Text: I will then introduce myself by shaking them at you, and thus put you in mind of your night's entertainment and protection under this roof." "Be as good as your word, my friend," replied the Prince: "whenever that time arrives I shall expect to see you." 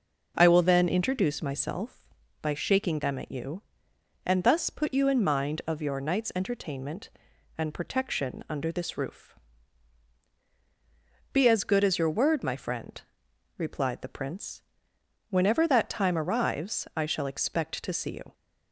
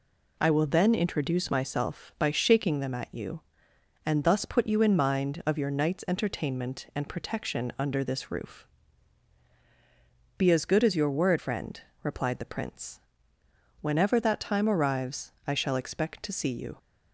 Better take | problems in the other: first | skips "my"; at 11.3 s

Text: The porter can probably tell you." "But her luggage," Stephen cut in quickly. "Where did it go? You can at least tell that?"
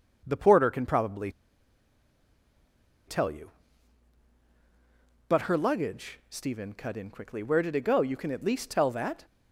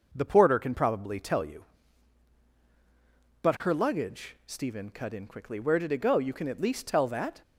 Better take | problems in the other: second | pauses between "probably" and "tell"; strong; at 1.3 s; 1.7 s long

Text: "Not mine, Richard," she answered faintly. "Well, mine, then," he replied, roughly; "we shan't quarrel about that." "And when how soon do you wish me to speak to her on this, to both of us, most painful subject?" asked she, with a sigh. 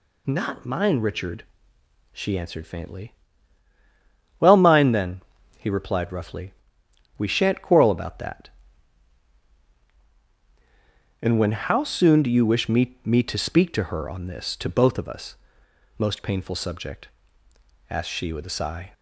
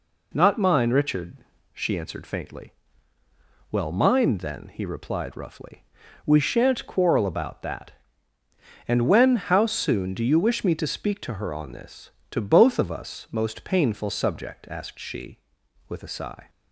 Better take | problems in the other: second | says "me" twice; at 13.0 s

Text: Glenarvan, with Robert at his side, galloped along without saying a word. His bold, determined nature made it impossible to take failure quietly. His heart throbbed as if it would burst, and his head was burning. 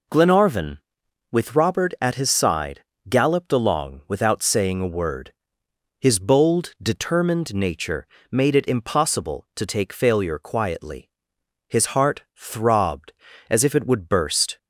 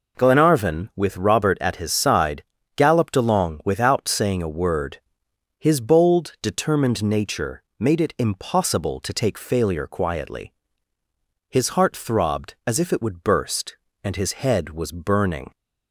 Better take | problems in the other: second | pauses between "nature" and "made"; slight; at 8.0 s; 0.24 s long; slight in the second // stops before "and his head was burning"; at 14.5 s

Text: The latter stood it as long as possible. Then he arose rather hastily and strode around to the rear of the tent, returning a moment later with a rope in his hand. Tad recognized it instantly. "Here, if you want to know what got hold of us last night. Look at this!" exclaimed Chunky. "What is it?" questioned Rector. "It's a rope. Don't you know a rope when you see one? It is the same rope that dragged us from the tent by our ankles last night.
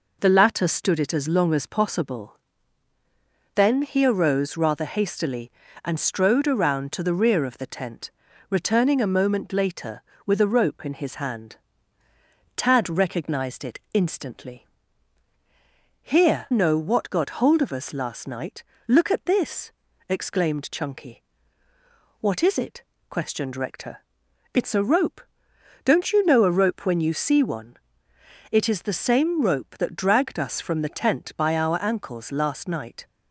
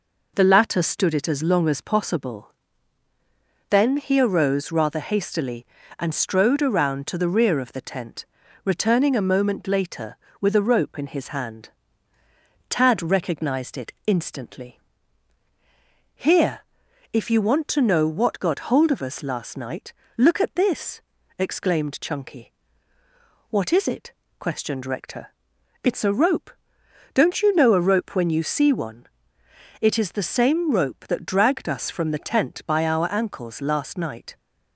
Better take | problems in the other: second | skips "if you want to"; at 16.5 s

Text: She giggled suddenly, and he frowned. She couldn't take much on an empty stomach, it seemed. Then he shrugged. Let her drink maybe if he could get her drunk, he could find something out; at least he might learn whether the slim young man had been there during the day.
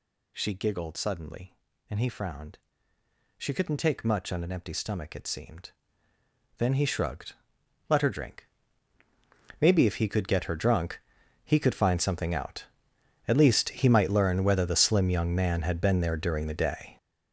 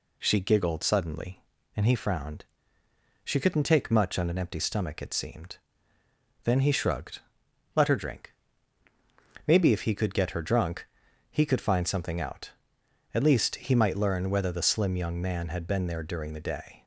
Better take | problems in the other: second | gets louder; strong; throughout; 10.5 dB // pauses between "drink" and "maybe"; at 8.4 s; 1.1 s long; also in the second

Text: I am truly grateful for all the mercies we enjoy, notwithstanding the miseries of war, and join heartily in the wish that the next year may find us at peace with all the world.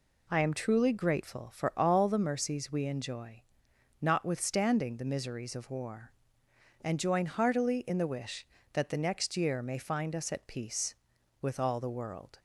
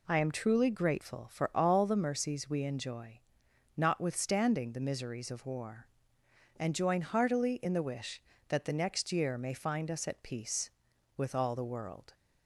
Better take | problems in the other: neither | none

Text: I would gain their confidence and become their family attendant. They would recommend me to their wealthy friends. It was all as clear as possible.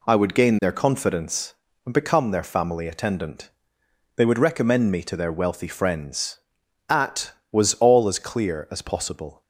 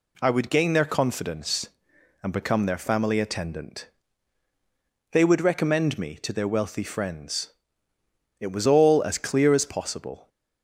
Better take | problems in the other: second | says "At" for "It"; at 6.8 s

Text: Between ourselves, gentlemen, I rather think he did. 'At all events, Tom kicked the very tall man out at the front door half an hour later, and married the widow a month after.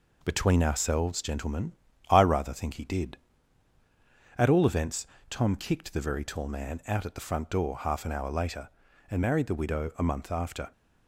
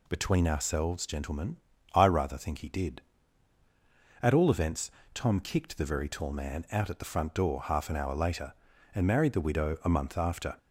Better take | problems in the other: second | gets quieter; slight; throughout; 3.5 dB

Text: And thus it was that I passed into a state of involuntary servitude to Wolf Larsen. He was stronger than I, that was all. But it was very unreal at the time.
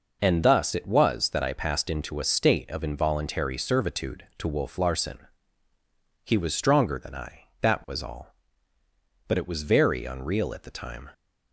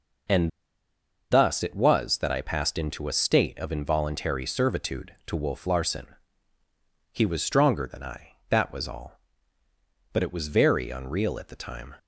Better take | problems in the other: first | pauses between "And" and "thus"; noticeable; at 0.4 s; 0.82 s long

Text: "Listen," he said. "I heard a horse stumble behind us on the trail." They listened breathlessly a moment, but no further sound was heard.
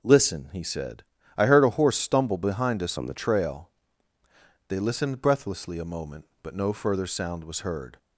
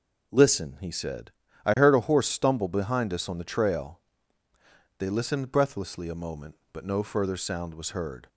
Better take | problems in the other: second | changes voice from "on" to "the"; from 2.9 to 3.1 s; 0.2 s long

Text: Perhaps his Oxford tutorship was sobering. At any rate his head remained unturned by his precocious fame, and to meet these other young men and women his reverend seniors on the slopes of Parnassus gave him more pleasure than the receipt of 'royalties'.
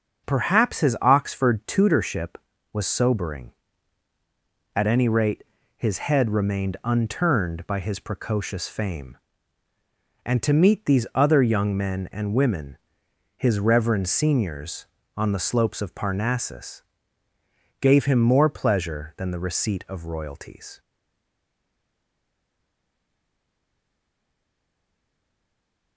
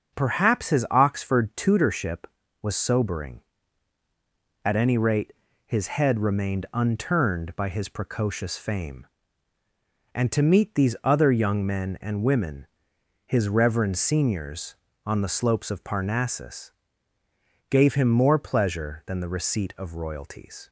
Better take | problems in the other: second | starts louder than the rest; until 1.3 s; 6.5 dB; also in the second // pauses between "rate" and "his"; slight; at 5.4 s; 0.32 s long; slight in the second // pauses between "women" and "his"; noticeable; at 12.7 s; 0.58 s long; noticeable in the second // pauses between "Parnassus" and "gave"; noticeable; at 16.8 s; 0.98 s long; noticeable in the second // stays silent after the last word; strong; from 20.7 s on; 5.2 s long

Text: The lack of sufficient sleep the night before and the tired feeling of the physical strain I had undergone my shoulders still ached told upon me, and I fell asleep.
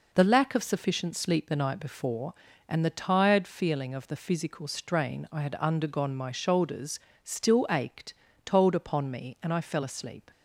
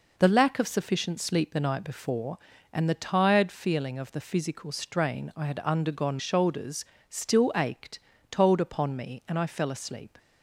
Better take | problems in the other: first | skips "my"; at 6.1 s // pauses between "shoulders" and "still"; slight; at 6.8 s; 0.24 s long; slight in the first // pauses between "ached" and "told"; slight; at 7.9 s; 0.32 s long; slight in the first

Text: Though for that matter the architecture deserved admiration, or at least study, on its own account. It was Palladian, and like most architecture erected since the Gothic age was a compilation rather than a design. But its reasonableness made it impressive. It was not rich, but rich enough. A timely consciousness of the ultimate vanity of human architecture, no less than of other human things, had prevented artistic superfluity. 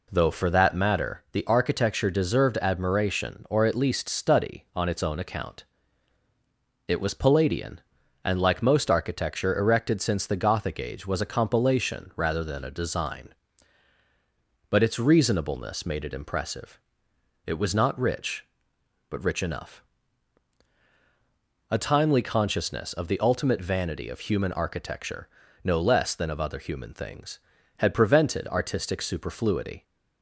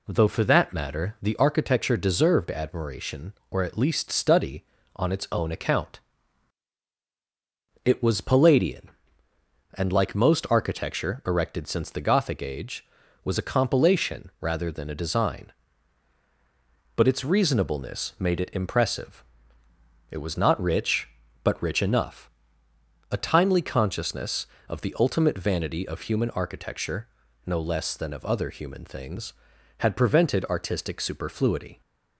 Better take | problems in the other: neither | none

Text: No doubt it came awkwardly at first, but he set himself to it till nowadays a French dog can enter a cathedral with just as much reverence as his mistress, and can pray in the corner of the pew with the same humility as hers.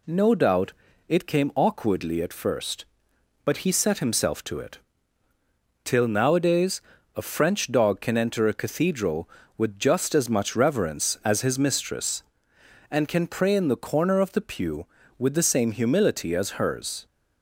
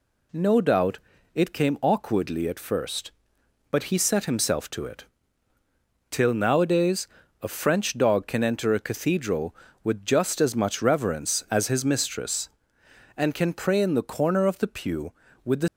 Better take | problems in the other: first | pauses between "doubt" and "it"; slight; at 0.9 s; 0.34 s long; slight in the first // pauses between "it" and "till"; at 5.0 s; 1.0 s long; also in the first // pauses between "nowadays" and "a"; at 7.0 s; 0.38 s long; also in the first // stops before "same humility as hers"; at 15.6 s

